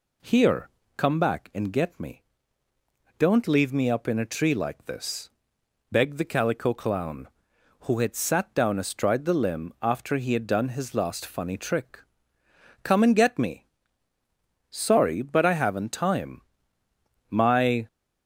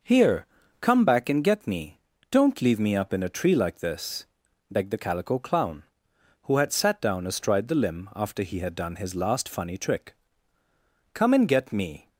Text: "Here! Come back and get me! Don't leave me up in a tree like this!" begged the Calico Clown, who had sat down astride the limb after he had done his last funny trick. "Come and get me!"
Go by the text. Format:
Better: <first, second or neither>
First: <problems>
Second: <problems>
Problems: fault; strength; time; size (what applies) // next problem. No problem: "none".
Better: second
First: goes on to say "Sorry but I haven't time My"; strong; from 14.6 s on; 3.1 s long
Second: none